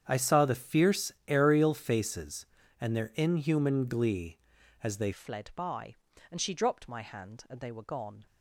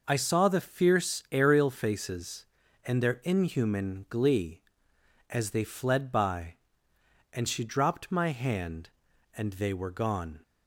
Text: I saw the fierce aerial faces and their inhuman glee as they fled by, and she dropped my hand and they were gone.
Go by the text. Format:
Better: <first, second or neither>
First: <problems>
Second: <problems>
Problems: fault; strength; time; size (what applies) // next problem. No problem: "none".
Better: second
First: starts louder than the rest; strong; until 1.1 s; 8.5 dB // pauses between "fierce" and "aerial"; slight; at 1.0 s; 0.16 s long // changes voice at "fled"; from 5.1 s on; 3.1 s long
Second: none